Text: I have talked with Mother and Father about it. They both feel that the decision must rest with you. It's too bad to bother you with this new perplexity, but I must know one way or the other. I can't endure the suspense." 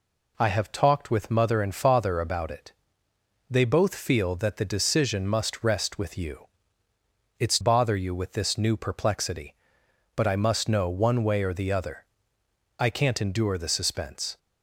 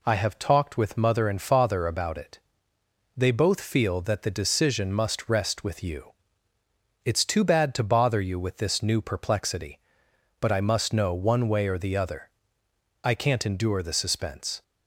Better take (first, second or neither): second